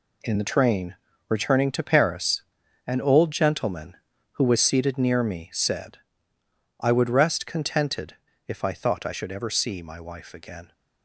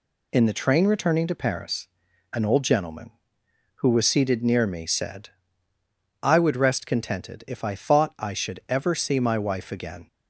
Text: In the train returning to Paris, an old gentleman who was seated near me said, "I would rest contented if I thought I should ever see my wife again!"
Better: second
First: gets quieter; strong; throughout; 9 dB // pauses between "train" and "returning"; slight; at 0.9 s; 0.34 s long // pauses between "contented" and "if"; slight; at 8.1 s; 0.30 s long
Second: none

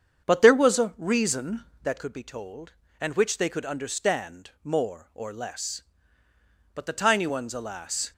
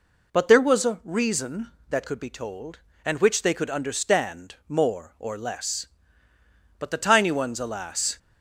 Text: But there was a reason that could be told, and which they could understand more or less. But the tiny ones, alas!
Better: second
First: starts louder than the rest; strong; until 2.0 s; 7.5 dB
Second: none

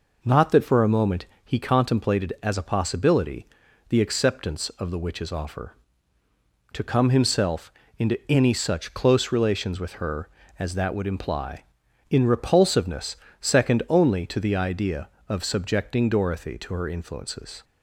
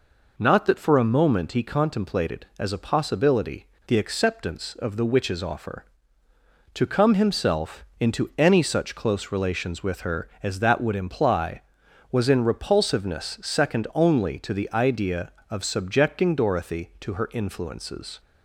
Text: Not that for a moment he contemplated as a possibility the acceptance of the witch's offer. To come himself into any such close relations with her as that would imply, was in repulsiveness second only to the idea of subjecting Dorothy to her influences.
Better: second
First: pauses between "moment" and "he"; slight; at 1.2 s; 0.20 s long // pauses between "possibility" and "the"; at 3.4 s; 0.42 s long // pauses between "himself" and "into"; slight; at 7.7 s; 0.26 s long // skips "was"; at 11.8 s // pauses between "repulsiveness" and "second"; slight; at 13.1 s; 0.24 s long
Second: pauses between "possibility" and "the"; slight; at 3.6 s; 0.21 s long

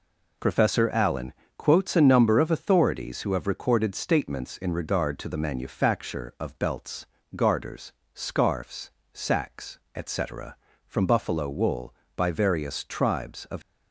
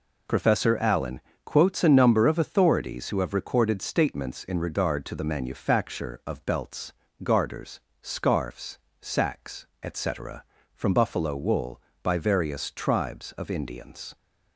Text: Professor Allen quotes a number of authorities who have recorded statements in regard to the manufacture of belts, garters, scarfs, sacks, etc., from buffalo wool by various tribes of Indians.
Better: second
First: pauses between "Allen" and "quotes"; slight; at 1.3 s; 0.24 s long // stops before "Indians"; at 13.6 s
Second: pauses between "Allen" and "quotes"; slight; at 1.2 s; 0.24 s long

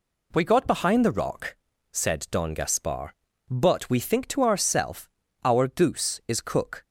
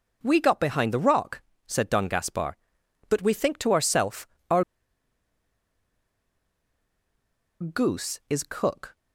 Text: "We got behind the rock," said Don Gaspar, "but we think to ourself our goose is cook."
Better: first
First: pauses between "ourself" and "our"; slight; at 5.0 s; 0.34 s long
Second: pauses between "ourself" and "our"; slight; at 4.2 s; 0.24 s long // pauses between "our" and "goose"; strong; at 4.6 s; 2.9 s long

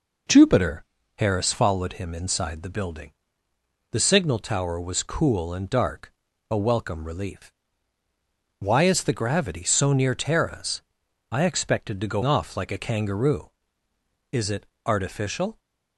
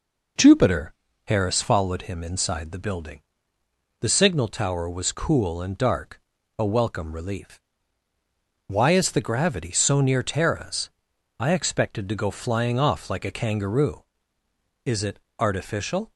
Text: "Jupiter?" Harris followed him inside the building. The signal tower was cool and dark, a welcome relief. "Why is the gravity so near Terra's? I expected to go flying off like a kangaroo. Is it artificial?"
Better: second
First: skips "flying"; at 12.2 s // pauses between "it" and "artificial"; slight; at 14.6 s; 0.20 s long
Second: pauses between "it" and "artificial"; slight; at 15.1 s; 0.20 s long

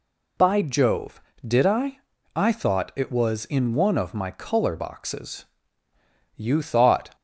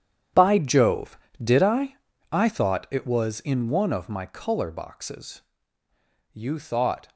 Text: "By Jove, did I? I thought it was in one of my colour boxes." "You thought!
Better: first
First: none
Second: gets quieter; strong; throughout; 16 dB

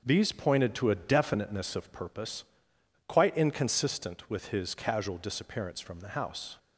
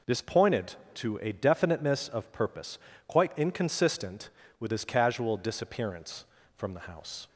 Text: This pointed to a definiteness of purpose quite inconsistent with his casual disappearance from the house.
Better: second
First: starts louder than the rest; noticeable; until 1.0 s; 6 dB // says "These" for "This"; at 0.0 s // pauses between "purpose" and "quite"; noticeable; at 2.4 s; 0.64 s long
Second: pauses between "purpose" and "quite"; slight; at 2.7 s; 0.30 s long

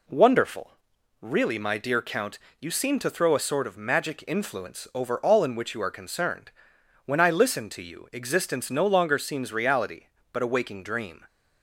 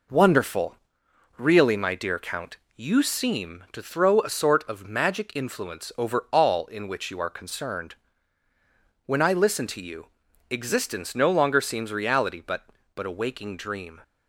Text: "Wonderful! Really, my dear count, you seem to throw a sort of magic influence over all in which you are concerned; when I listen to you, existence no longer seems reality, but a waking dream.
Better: first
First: none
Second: says "but" twice; at 12.9 s

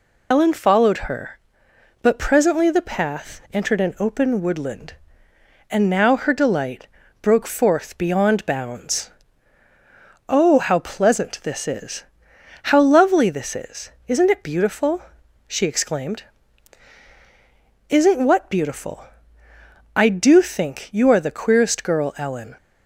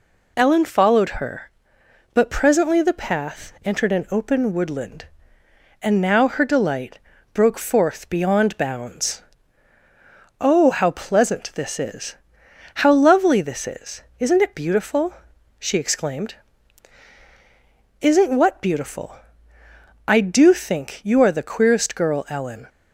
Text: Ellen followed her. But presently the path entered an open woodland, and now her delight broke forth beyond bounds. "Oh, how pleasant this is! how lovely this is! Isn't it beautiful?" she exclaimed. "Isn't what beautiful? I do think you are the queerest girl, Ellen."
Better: second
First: loses the start of "Ellen"; at 0.3 s; 60 ms // pauses between "delight" and "broke"; slight; at 6.8 s; 0.34 s long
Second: pauses between "delight" and "broke"; slight; at 6.9 s; 0.34 s long

